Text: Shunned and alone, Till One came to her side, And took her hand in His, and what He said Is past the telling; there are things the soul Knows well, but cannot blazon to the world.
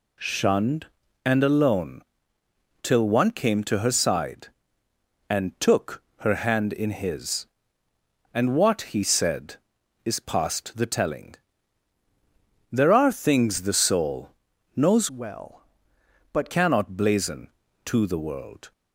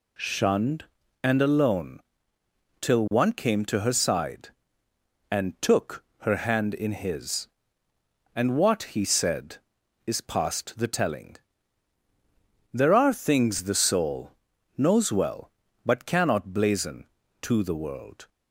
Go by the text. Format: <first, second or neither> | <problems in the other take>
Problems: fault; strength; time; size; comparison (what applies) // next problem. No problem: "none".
second | pauses between "took" and "her"; slight; at 6.0 s; 0.16 s long; slight in the second // pauses between "soul" and "Knows"; at 14.3 s; 0.44 s long; also in the second // changes voice from "well" to "but"; from 15.1 to 16.5 s; 1.4 s long